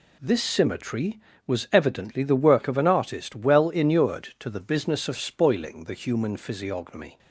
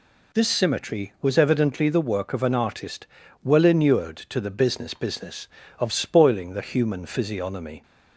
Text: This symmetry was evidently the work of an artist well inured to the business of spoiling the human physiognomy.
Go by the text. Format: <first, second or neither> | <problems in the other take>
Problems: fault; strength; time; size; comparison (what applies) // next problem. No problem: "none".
first | pauses between "artist" and "well"; slight; at 3.0 s; 0.34 s long // says "business" twice; at 4.9 s